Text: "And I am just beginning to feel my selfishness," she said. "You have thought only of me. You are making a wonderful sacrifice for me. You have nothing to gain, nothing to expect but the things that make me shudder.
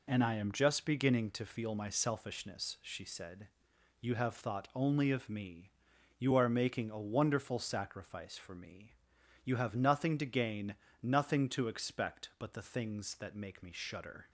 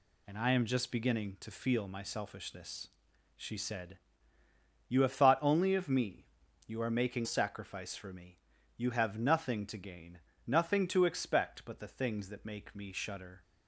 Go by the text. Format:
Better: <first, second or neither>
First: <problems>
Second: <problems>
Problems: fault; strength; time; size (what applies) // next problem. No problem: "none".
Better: first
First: none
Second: skips "a wonderful"; at 7.2 s